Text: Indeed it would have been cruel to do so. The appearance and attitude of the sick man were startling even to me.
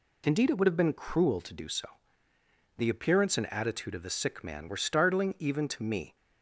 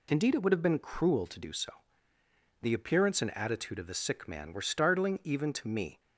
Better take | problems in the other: neither | none

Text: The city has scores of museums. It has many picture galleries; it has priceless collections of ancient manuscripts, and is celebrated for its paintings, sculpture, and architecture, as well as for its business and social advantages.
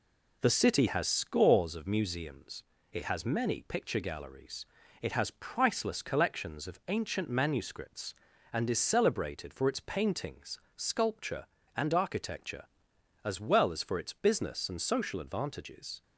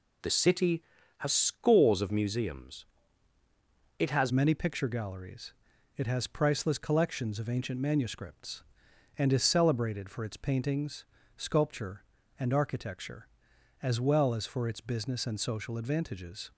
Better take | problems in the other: first | changes voice at "many"; from 4.3 s on; 12.2 s long

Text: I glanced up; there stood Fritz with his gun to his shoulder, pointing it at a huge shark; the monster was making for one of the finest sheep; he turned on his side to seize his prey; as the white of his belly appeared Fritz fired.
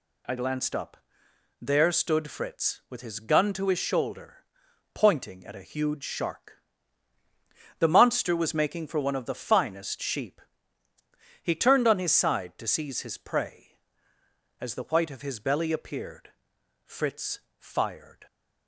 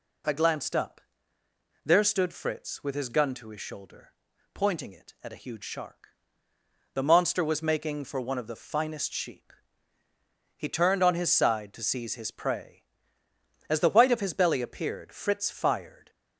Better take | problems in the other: second | skips "it"; at 5.4 s // pauses between "appeared" and "Fritz"; noticeable; at 16.3 s; 0.54 s long // pauses between "Fritz" and "fired"; slight; at 17.3 s; 0.22 s long

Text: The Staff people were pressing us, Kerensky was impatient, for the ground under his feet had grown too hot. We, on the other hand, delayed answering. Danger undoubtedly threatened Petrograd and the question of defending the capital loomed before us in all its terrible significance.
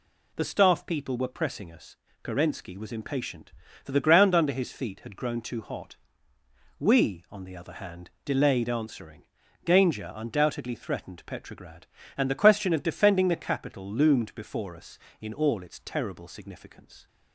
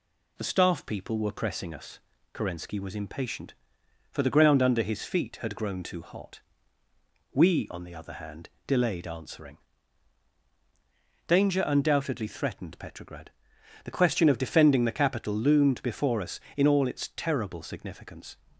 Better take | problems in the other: first | skips "and"; at 13.5 s

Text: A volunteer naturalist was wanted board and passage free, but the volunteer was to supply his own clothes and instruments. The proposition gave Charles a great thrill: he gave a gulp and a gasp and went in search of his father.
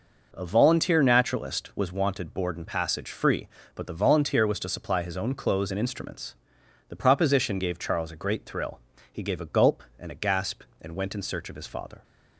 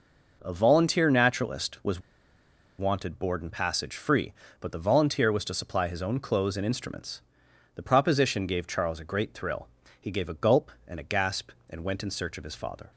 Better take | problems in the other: first | pauses between "was" and "wanted"; noticeable; at 1.9 s; 0.78 s long

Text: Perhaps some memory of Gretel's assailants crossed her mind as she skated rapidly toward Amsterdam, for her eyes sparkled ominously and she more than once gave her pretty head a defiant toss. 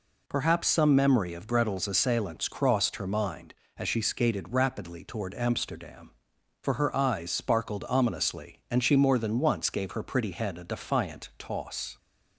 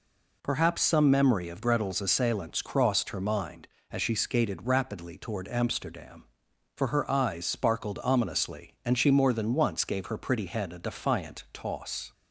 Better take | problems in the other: neither | none

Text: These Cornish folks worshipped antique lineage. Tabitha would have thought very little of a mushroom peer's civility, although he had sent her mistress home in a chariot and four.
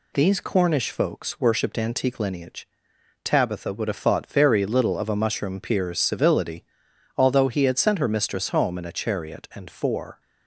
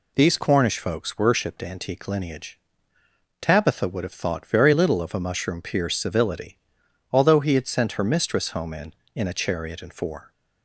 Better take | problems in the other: first | says "in" twice; at 9.1 s

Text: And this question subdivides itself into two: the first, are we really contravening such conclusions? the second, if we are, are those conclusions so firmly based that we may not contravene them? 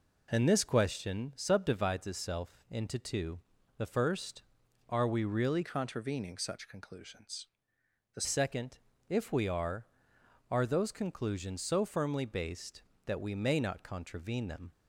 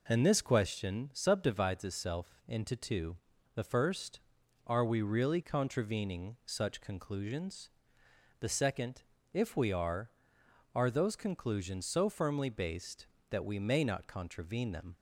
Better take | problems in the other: second | changes voice from "contravening" to "the"; from 5.6 to 8.2 s; 2.6 s long

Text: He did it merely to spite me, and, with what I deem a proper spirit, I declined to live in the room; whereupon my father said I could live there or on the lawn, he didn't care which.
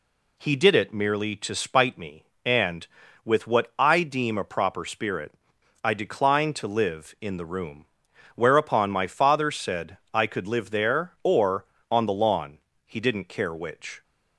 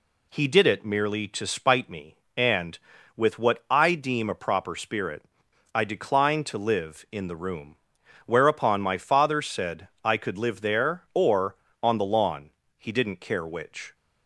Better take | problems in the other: neither | pauses between "said" and "I"; slight; the same in both

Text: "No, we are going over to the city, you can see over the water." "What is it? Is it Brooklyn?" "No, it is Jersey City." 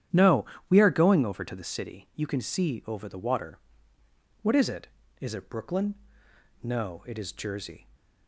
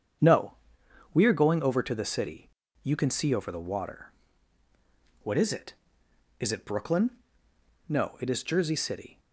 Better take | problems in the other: second | starts louder than the rest; strong; until 1.3 s; 10 dB; strong in the second // stops before "City"; at 7.9 s

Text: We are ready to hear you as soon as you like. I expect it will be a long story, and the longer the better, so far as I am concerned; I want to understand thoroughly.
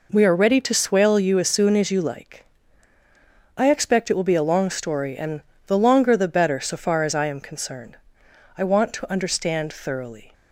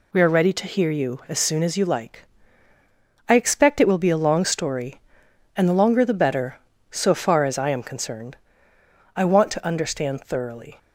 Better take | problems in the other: second | says "swale" for "hear"; at 0.7 s // pauses between "and" and "the"; slight; at 5.4 s; 0.24 s long

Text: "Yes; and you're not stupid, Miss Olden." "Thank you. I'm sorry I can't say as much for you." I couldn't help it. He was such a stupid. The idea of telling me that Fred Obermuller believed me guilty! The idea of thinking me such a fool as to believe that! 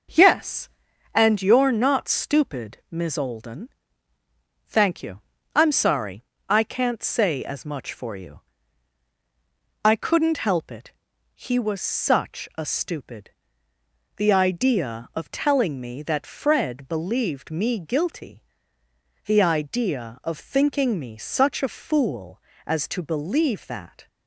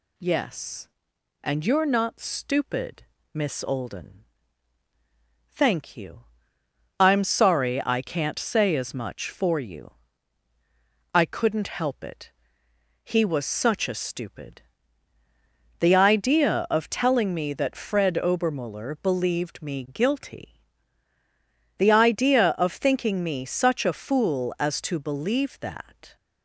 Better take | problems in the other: second | pauses between "sorry" and "I"; slight; at 6.2 s; 0.24 s long // skips "Obermuller"; at 16.8 s

